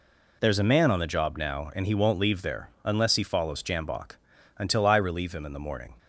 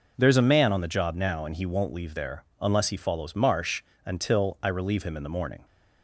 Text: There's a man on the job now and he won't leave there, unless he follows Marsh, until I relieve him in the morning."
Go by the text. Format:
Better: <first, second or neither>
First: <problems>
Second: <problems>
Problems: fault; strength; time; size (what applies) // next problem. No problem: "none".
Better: second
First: says "Jambok" for "Marsh"; at 3.6 s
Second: none